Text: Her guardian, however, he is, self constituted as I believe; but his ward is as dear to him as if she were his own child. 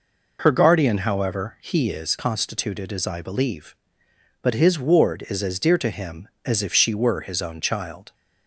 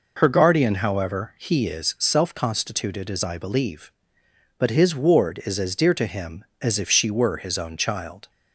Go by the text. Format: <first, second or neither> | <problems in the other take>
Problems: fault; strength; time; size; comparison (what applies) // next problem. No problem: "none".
second | skips "self"; at 2.1 s